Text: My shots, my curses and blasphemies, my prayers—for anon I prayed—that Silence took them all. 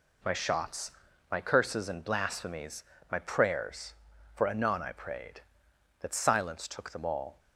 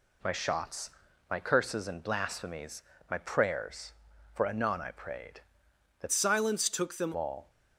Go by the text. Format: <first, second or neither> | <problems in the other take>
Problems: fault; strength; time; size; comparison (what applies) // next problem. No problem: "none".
first | changes voice from "Silence" to "them"; from 6.1 to 7.1 s; 1.0 s long